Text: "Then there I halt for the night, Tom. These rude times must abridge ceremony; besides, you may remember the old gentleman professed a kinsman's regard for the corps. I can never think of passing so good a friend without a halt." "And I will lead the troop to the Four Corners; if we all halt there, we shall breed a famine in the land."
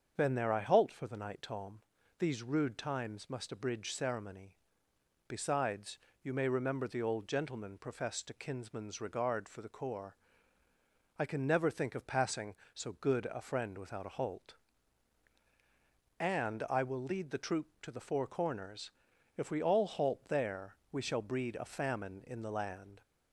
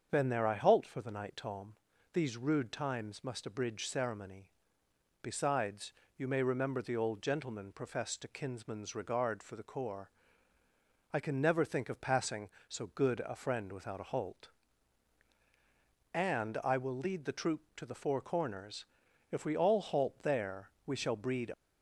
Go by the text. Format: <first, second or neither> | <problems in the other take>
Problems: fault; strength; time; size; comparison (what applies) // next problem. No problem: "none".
first | starts louder than the rest; until 1.1 s; 7 dB; also in the first // stops before "a famine in the land"; at 21.5 s